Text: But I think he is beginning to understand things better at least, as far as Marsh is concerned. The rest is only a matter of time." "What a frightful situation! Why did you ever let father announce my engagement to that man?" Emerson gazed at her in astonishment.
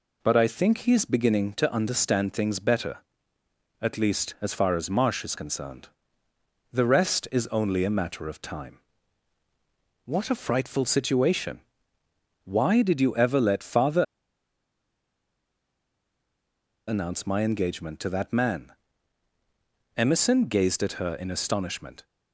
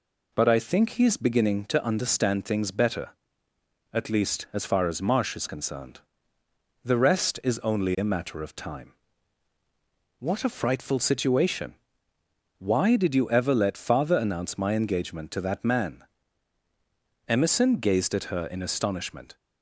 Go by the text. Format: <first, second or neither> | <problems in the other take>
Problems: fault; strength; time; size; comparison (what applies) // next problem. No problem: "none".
second | pauses between "father" and "announce"; strong; at 14.0 s; 2.8 s long